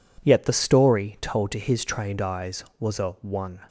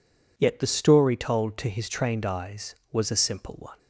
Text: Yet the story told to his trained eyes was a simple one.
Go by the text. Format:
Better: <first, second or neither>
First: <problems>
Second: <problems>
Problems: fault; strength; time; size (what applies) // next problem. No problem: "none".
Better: second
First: skips "simple"; at 3.1 s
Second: none